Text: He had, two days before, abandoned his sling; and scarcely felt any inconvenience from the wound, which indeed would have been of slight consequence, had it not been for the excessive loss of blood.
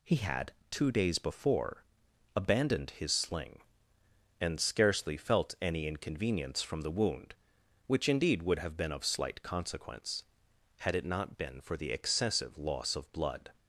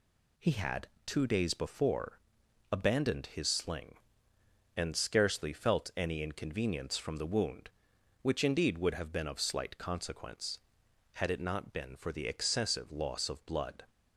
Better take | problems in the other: neither | none

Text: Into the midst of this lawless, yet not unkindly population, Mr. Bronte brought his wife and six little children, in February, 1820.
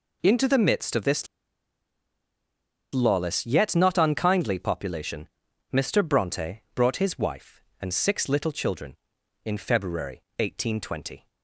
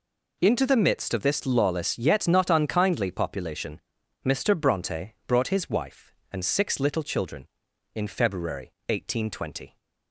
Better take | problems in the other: second | pauses between "this" and "lawless"; strong; at 1.2 s; 1.6 s long

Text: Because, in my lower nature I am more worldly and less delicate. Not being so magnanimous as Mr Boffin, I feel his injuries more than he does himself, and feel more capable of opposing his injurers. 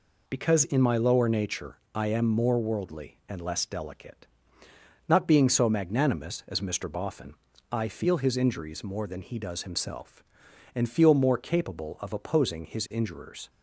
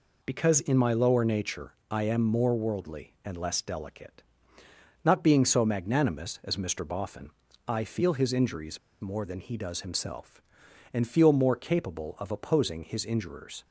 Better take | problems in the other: first | pauses between "nature" and "I"; slight; at 1.7 s; 0.16 s long; slight in the first // pauses between "injuries" and "more"; slight; at 8.7 s; 0.23 s long

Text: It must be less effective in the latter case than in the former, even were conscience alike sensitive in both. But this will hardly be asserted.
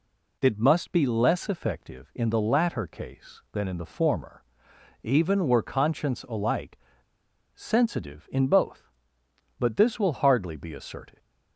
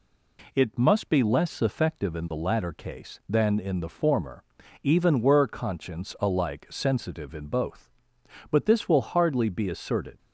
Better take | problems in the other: second | pauses between "alike" and "sensitive"; noticeable; at 6.7 s; 0.78 s long

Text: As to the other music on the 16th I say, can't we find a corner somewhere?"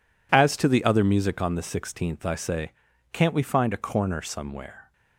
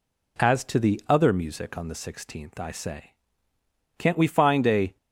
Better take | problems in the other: first | stops before "corner somewhere"; at 4.9 s

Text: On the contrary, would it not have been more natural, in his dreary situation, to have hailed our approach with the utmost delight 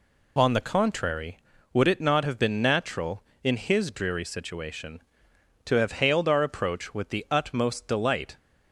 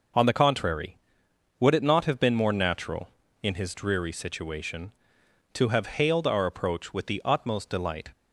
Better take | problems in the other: second | skips "more"; at 2.6 s

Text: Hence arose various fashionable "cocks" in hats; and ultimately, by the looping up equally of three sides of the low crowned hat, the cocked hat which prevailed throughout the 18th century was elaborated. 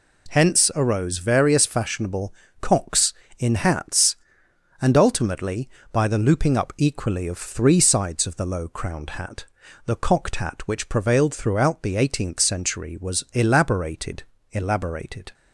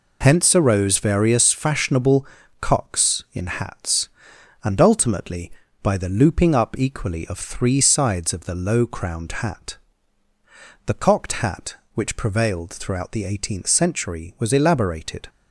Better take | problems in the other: second | pauses between "fashionable" and "cocks"; slight; at 2.3 s; 0.26 s long; slight in the second // says "elaborated" twice; at 14.5 s

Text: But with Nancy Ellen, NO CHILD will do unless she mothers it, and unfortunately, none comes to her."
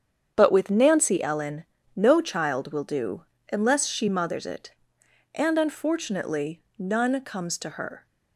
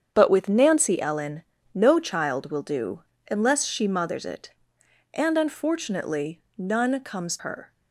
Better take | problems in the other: first | starts louder than the rest; strong; until 1.1 s; 8 dB; strong in the first // pauses between "do" and "unless"; slight; at 3.0 s; 0.28 s long; slight in the first // skips "to"; at 7.3 s

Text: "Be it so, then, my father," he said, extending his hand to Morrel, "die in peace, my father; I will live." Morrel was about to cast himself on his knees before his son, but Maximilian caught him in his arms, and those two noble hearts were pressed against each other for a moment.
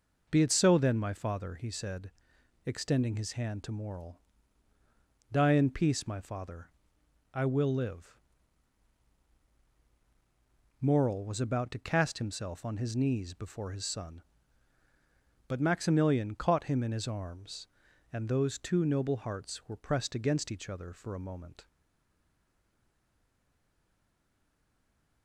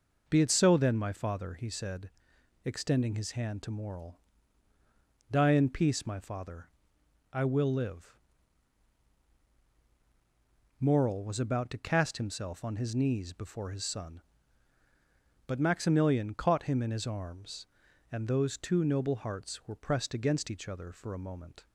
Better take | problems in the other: second | stays silent after the last word; strong; from 21.6 s on; 3.6 s long

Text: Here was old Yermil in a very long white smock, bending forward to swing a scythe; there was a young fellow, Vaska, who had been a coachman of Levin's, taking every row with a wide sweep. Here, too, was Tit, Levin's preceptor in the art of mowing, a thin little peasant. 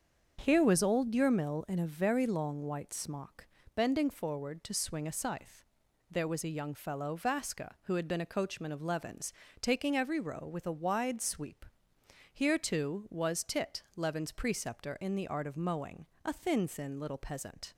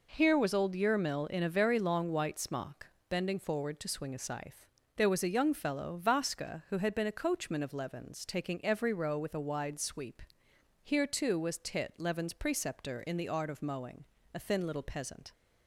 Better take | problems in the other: second | starts louder than the rest; until 1.4 s; 7 dB // says "thin" twice; at 16.6 s

